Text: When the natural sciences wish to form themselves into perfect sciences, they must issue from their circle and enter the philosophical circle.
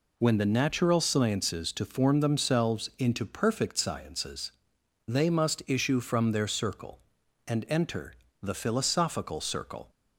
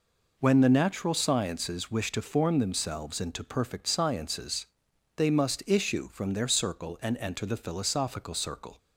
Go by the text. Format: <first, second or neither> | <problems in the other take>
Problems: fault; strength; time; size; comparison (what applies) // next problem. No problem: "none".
second | skips "wish"; at 1.7 s // pauses between "enter" and "the"; slight; at 8.1 s; 0.28 s long